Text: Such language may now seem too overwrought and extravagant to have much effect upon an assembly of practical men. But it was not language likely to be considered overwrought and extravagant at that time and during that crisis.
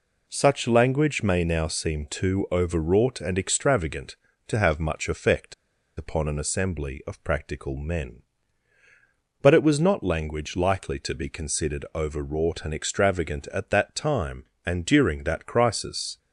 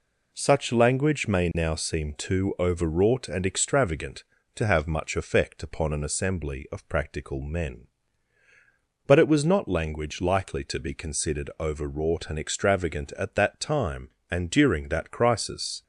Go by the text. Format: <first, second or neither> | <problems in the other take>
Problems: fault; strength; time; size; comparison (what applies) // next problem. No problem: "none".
second | pauses between "effect" and "upon"; at 5.5 s; 0.43 s long